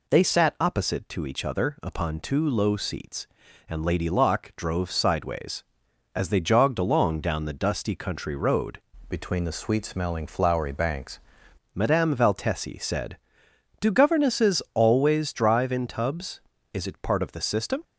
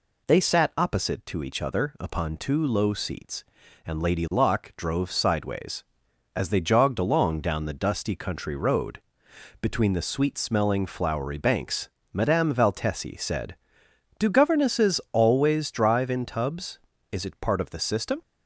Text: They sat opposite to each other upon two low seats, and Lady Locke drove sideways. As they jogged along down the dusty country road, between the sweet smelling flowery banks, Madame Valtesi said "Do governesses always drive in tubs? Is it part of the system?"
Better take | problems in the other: second | changes voice from "between" to "banks"; from 9.0 to 11.2 s; 2.2 s long

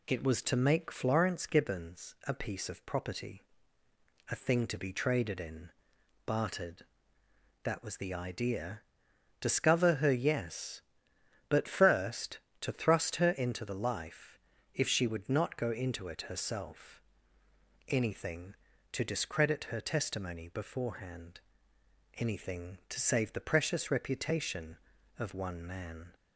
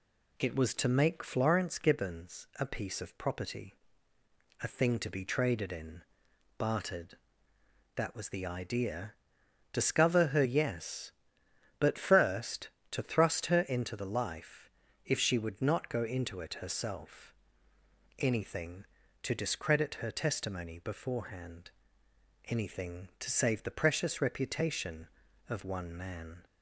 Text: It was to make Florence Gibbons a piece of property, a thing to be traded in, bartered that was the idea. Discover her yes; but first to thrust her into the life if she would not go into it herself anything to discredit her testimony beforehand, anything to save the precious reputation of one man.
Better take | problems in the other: neither | pauses between "life" and "if"; the same in both // pauses between "herself" and "anything"; noticeable; the same in both

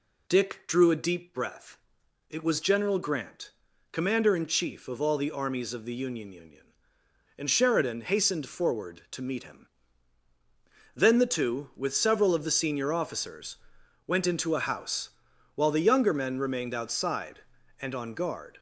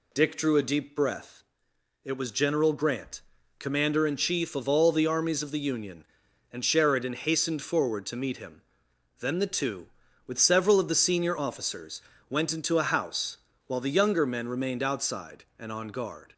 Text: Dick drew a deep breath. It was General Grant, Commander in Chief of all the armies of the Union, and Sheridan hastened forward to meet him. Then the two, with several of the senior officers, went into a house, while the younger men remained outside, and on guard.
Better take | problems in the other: second | says "Union" twice; at 6.3 s

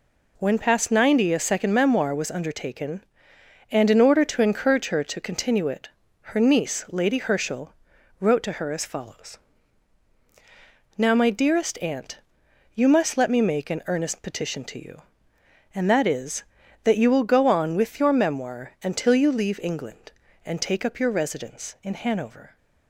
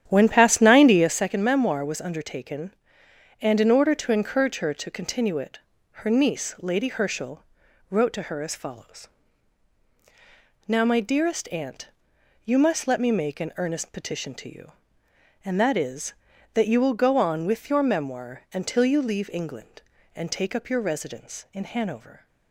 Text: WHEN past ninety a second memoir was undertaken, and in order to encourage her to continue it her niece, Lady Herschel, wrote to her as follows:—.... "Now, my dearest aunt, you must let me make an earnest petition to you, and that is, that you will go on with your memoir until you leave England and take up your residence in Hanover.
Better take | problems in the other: first | starts louder than the rest; strong; until 1.2 s; 10 dB // pauses between "it" and "her"; at 5.5 s; 0.44 s long; also in the first

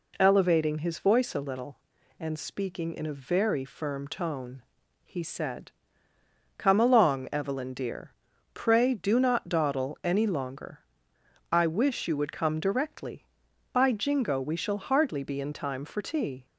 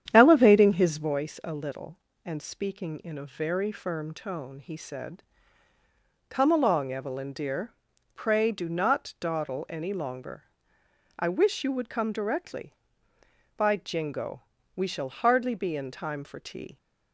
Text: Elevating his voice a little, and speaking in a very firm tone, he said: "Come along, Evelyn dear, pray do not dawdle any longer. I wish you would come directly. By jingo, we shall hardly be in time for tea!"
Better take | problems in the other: first | starts louder than the rest; strong; until 1.2 s; 9.5 dB

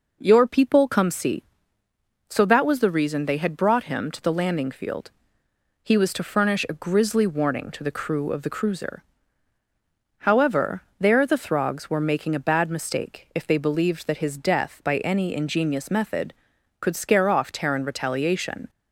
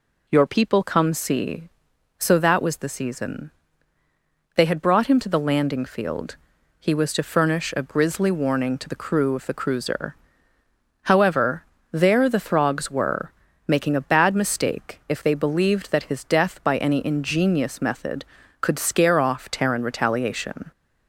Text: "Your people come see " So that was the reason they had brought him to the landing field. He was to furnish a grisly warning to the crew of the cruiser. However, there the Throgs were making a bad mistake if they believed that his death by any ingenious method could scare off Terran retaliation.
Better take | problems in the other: first | says "season" for "reason"; at 2.8 s // pauses between "were" and "making"; slight; at 13.3 s; 0.36 s long

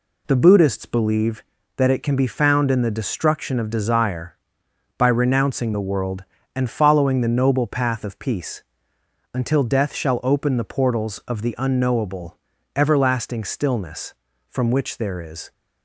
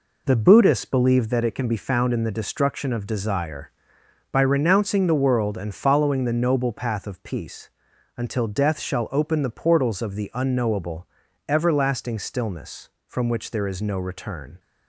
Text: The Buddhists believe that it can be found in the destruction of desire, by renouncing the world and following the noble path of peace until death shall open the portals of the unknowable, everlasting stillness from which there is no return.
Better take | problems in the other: second | pauses between "peace" and "until"; noticeable; at 8.6 s; 0.72 s long; noticeable in the second // stops before "no return"; at 15.5 s

